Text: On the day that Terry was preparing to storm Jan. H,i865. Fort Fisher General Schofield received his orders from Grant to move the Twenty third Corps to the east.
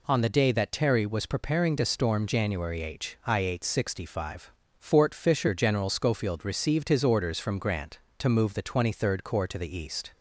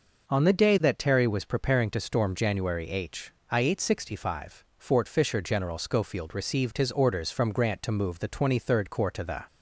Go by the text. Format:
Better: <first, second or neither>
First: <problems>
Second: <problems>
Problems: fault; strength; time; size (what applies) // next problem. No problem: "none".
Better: first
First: none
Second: stops before "east"; at 9.4 s